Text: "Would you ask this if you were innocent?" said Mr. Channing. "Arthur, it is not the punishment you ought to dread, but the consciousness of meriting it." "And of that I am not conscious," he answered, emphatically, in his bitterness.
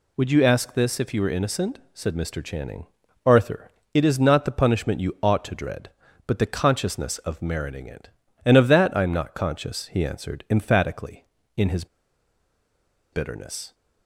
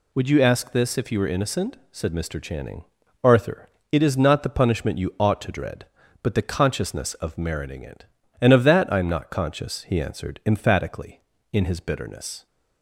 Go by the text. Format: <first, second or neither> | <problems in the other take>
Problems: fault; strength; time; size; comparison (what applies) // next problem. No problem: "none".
second | pauses between "his" and "bitterness"; strong; at 11.8 s; 1.2 s long